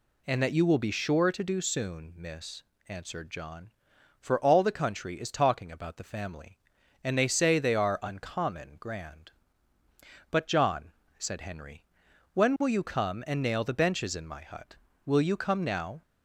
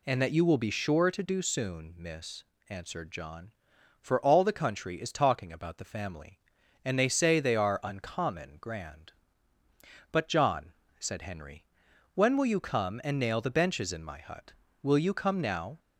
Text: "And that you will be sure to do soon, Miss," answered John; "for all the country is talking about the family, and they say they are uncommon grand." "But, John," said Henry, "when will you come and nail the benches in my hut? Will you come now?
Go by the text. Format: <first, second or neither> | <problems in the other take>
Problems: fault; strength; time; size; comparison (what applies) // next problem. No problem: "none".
neither | none